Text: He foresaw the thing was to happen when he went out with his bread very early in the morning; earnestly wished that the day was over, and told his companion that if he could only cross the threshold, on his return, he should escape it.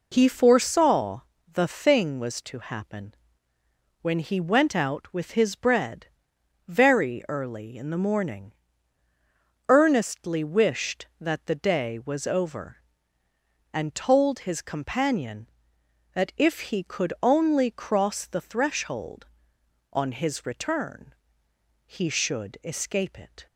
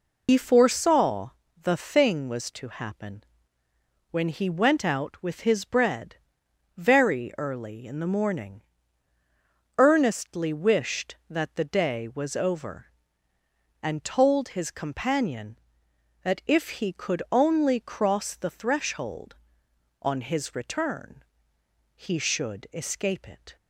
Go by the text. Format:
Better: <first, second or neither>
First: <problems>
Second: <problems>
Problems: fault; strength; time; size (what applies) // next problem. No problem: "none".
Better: first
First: pauses between "foresaw" and "the"; slight; at 1.2 s; 0.30 s long // pauses between "happen" and "when"; noticeable; at 3.1 s; 0.88 s long // pauses between "bread" and "very"; noticeable; at 6.0 s; 0.62 s long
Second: loses the start of "He"; at 0.2 s; 80 ms // pauses between "foresaw" and "the"; slight; at 1.2 s; 0.30 s long // pauses between "happen" and "when"; noticeable; at 3.2 s; 0.88 s long // pauses between "bread" and "very"; noticeable; at 6.1 s; 0.62 s long